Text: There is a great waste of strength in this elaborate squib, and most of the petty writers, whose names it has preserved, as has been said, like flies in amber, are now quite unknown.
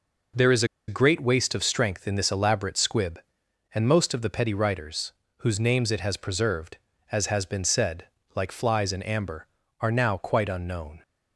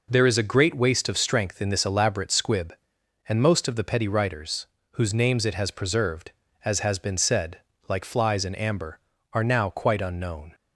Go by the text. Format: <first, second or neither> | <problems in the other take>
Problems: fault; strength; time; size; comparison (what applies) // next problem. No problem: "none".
second | pauses between "is" and "a"; slight; at 0.6 s; 0.23 s long